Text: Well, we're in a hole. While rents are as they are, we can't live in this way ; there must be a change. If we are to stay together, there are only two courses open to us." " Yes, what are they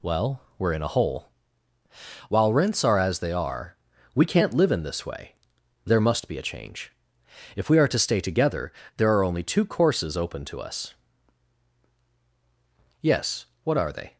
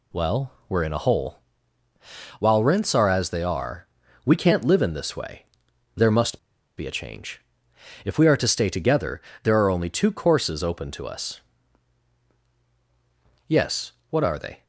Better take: first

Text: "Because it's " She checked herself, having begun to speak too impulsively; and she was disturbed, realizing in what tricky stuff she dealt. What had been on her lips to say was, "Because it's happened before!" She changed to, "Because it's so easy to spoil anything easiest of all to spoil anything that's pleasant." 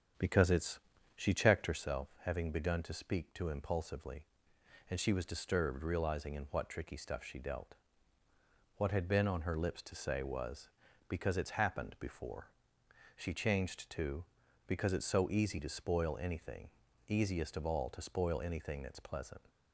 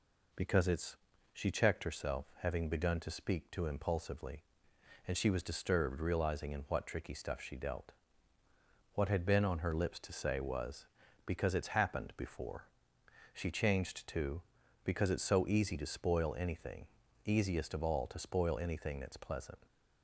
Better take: second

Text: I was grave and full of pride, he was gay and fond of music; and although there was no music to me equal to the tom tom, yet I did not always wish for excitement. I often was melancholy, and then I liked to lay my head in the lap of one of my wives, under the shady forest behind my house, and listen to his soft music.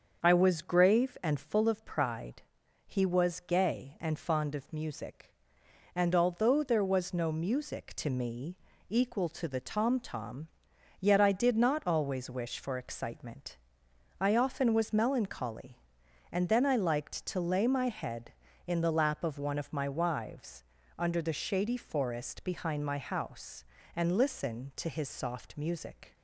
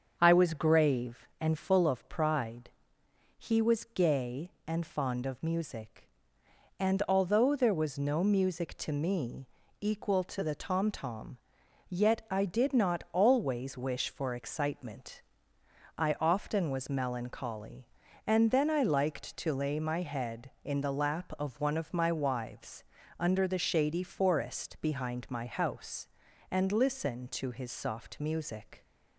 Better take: neither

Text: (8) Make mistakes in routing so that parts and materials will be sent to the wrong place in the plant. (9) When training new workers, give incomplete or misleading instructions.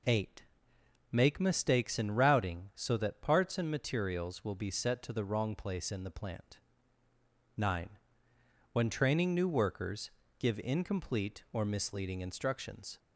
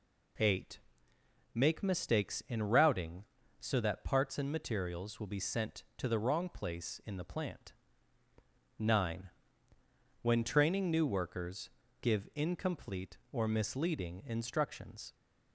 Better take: second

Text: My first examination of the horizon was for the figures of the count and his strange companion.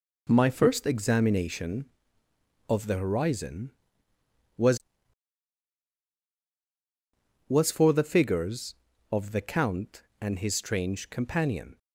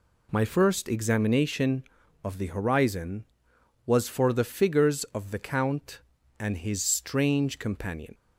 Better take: second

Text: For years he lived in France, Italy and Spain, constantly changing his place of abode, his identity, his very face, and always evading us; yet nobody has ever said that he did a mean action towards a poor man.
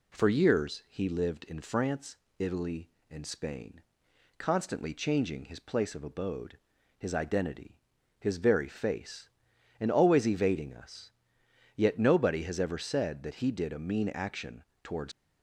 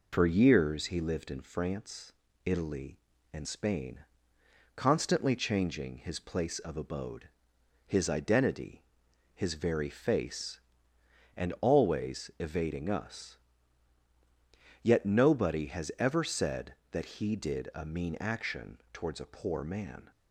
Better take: second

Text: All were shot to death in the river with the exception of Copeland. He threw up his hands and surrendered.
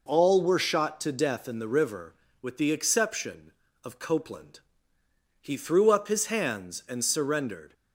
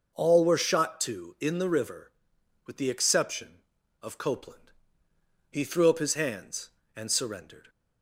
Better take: first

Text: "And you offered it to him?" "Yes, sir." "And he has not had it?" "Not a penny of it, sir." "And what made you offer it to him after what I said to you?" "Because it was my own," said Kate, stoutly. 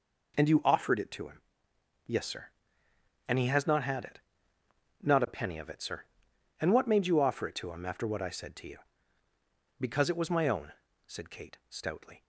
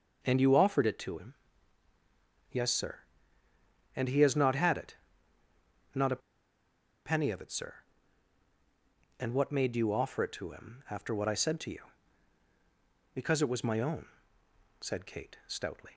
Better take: first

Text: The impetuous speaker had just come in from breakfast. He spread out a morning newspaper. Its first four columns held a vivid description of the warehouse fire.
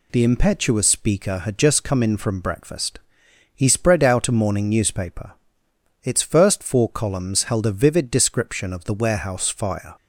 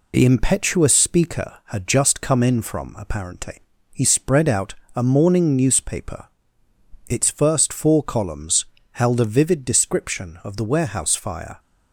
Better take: first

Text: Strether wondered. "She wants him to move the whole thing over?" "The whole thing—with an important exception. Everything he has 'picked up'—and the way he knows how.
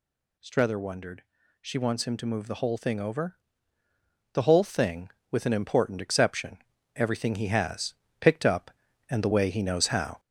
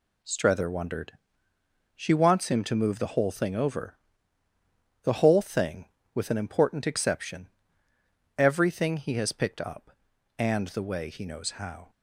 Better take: second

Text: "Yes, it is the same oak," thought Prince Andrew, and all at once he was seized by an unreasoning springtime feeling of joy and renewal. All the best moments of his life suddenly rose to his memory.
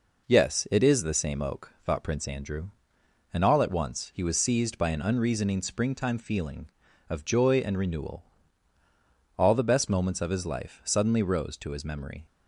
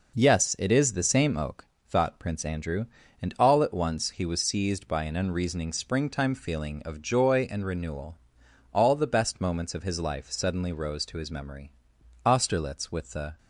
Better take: first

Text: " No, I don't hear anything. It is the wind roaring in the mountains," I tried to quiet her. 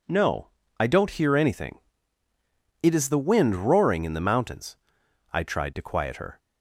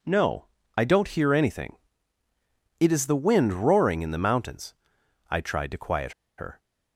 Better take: first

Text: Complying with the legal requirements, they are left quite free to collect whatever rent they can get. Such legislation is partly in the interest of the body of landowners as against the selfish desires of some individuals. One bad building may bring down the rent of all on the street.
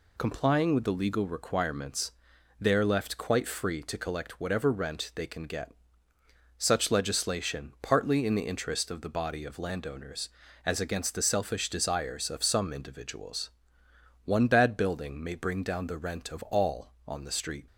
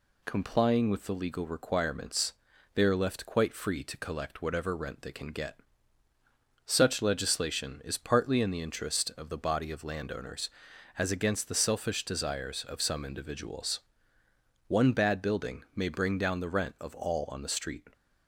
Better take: second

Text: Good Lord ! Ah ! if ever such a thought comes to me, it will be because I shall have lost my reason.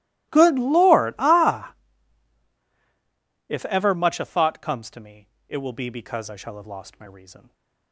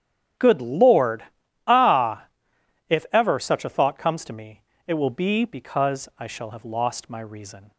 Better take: second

